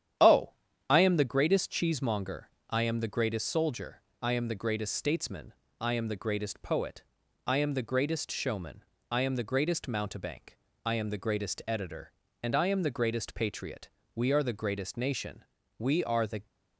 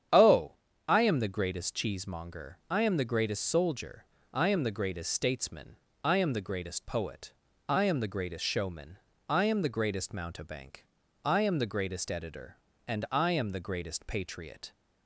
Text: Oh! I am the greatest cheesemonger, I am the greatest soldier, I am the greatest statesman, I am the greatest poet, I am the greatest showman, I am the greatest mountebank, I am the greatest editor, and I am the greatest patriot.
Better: second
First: starts louder than the rest; strong; until 1.5 s; 10 dB // goes on to say "We are the greatest nation We are the"; strong; from 14.1 s on; 2.3 s long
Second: starts louder than the rest; strong; until 1.4 s; 8.5 dB

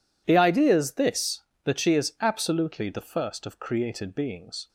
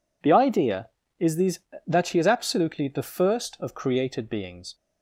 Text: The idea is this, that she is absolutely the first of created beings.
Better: first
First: none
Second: says "these" for "this"; at 1.3 s

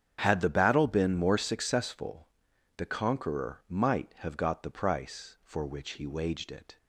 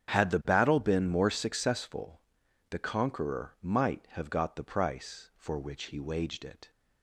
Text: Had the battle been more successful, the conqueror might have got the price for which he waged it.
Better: neither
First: starts louder than the rest; strong; until 1.2 s; 8 dB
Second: starts louder than the rest; strong; until 1.1 s; 8 dB

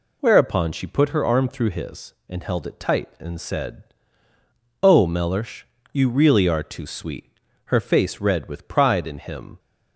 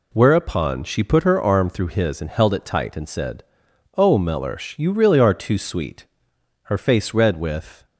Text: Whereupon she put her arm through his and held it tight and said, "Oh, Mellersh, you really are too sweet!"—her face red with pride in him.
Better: first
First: none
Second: stops before "pride in him"; at 7.8 s

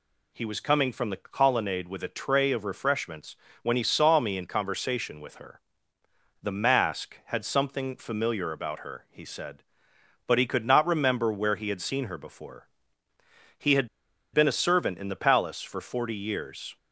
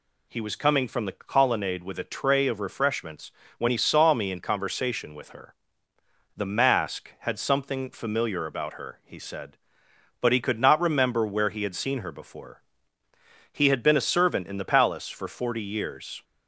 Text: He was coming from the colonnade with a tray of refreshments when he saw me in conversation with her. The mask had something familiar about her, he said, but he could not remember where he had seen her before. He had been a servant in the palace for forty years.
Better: second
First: pauses between "refreshments" and "when"; slight; at 3.3 s; 0.26 s long // pauses between "had" and "been"; noticeable; at 13.8 s; 0.46 s long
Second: pauses between "refreshments" and "when"; slight; at 3.3 s; 0.26 s long

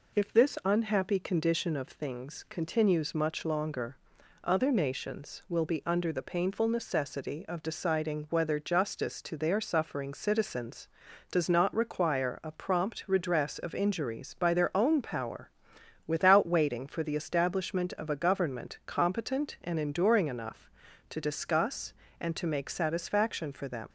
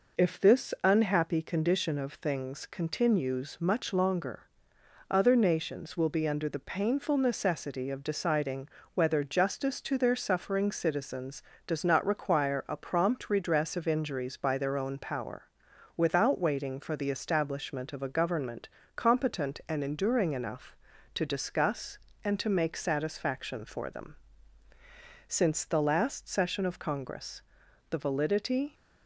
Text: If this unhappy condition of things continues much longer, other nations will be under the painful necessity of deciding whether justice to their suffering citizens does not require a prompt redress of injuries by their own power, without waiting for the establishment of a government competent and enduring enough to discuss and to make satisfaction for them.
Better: first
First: none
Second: pauses between "deciding" and "whether"; slight; at 8.6 s; 0.26 s long // pauses between "government" and "competent"; slight; at 18.6 s; 0.26 s long // goes on to say "Since the last session of Congress the validity"; strong; from 25.2 s on; 3.4 s long

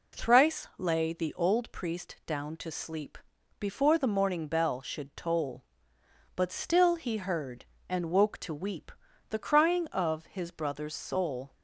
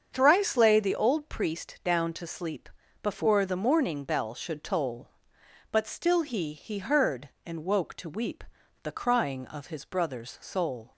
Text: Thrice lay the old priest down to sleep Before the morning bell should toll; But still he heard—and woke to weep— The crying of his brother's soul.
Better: first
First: pauses between "sleep" and "Before"; at 3.1 s; 0.40 s long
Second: starts louder than the rest; strong; until 1.1 s; 7 dB // pauses between "sleep" and "Before"; slight; at 2.6 s; 0.34 s long // says "he" twice; at 6.5 s

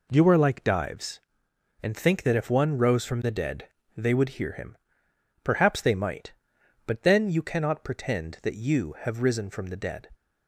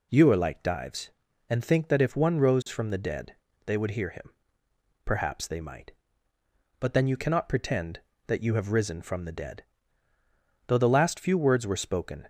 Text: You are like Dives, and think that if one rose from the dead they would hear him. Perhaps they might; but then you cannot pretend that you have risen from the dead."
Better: first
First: pauses between "dead" and "they"; slight; at 3.6 s; 0.30 s long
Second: pauses between "dead" and "they"; slight; at 3.3 s; 0.30 s long // goes on to say "Though the last few words were spoken"; from 10.6 s on; 1.6 s long

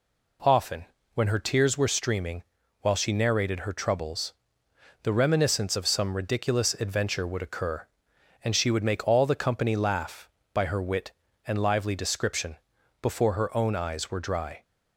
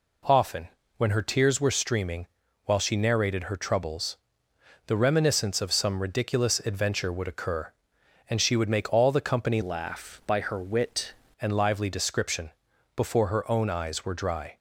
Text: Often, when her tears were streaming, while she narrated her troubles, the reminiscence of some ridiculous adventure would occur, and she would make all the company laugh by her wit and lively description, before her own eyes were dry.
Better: first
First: none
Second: changes voice from "laugh" to "wit"; from 9.6 to 11.1 s; 1.5 s long

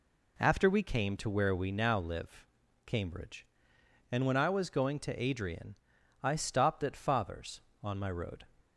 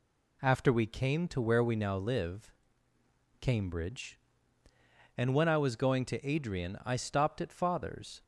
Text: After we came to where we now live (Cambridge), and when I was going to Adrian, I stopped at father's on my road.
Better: first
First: none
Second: stops before "on my road"; at 8.2 s

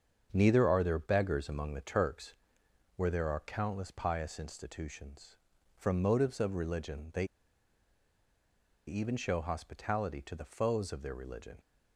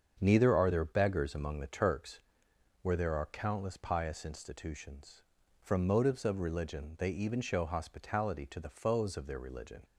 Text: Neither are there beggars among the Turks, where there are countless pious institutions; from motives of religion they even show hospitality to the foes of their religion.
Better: second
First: starts louder than the rest; until 1.3 s; 7 dB // pauses between "they" and "even"; strong; at 7.2 s; 1.6 s long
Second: starts louder than the rest; until 1.2 s; 7 dB

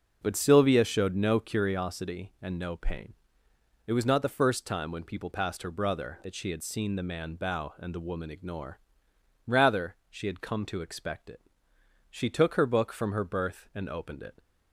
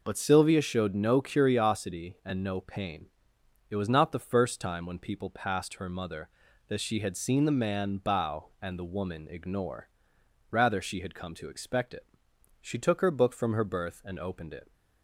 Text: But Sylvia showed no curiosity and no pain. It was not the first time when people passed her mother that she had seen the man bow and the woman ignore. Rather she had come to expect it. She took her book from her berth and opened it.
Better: second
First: says "brother" for "mother"; at 5.7 s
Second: none

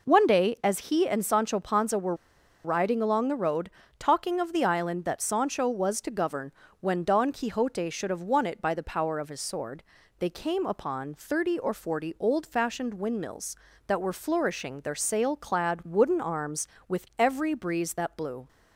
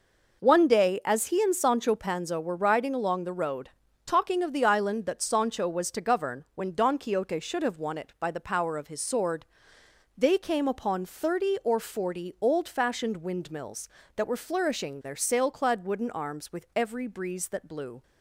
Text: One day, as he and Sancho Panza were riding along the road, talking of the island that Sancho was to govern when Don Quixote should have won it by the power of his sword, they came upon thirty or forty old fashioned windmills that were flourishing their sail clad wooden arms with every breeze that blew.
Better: second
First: pauses between "were" and "riding"; noticeable; at 2.1 s; 0.50 s long // pauses between "govern" and "when"; slight; at 6.5 s; 0.30 s long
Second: none

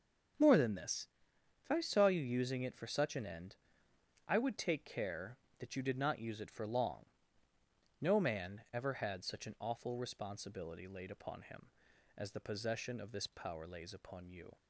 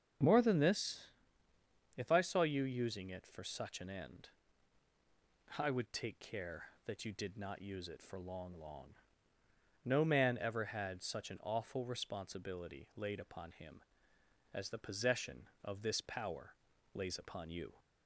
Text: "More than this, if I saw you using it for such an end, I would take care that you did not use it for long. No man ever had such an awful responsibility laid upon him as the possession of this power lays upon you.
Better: first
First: starts louder than the rest; until 1.9 s; 6.5 dB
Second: starts louder than the rest; until 2.1 s; 6.5 dB // says "long" twice; at 8.5 s // pauses between "power" and "lays"; slight; at 16.5 s; 0.36 s long

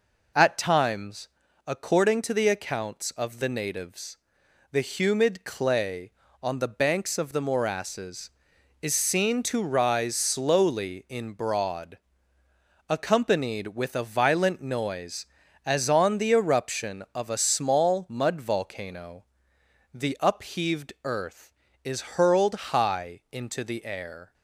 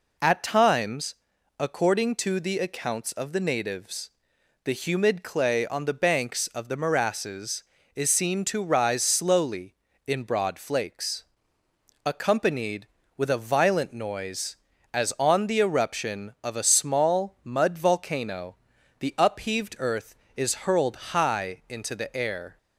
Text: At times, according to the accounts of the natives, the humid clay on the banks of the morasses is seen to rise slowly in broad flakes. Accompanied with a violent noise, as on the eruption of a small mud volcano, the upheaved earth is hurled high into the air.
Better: second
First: skips "flakes"; at 12.4 s // pauses between "hurled" and "high"; slight; at 22.5 s; 0.18 s long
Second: pauses between "hurled" and "high"; slight; at 20.9 s; 0.16 s long

